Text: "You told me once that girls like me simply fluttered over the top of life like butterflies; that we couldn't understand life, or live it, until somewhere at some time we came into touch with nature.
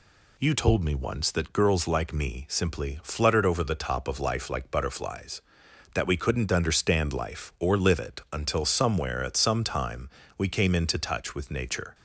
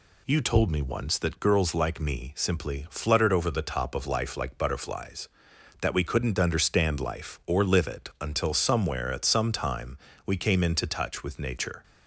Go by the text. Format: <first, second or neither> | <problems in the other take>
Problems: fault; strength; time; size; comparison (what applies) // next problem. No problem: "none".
neither | pauses between "time" and "we"; slight; the same in both